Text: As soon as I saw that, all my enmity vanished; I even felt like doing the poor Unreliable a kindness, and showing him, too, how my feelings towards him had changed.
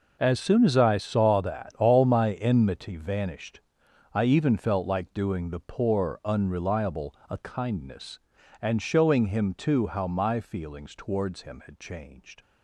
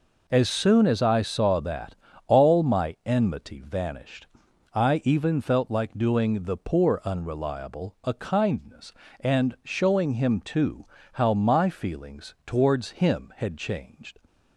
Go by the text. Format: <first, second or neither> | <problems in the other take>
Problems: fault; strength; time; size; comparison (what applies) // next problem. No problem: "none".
second | gets quieter; strong; throughout; 13.5 dB // pauses between "Unreliable" and "a"; slight; at 7.1 s; 0.16 s long